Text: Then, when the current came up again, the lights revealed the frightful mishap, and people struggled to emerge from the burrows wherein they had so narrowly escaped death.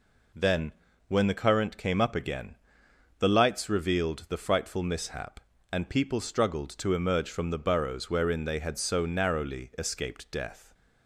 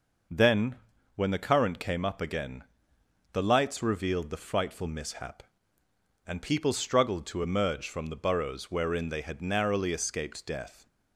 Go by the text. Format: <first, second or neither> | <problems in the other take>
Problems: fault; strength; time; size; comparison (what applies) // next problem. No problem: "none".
first | skips "so"; at 9.4 s